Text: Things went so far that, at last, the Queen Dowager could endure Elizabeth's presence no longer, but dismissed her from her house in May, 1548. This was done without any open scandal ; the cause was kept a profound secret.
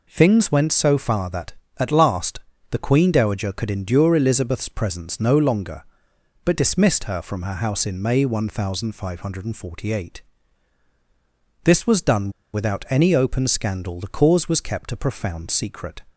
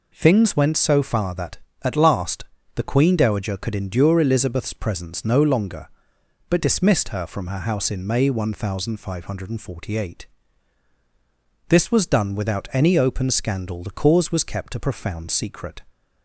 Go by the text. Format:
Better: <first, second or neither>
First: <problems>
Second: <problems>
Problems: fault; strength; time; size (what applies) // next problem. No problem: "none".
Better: second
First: pauses between "done" and "without"; slight; at 12.2 s; 0.24 s long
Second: none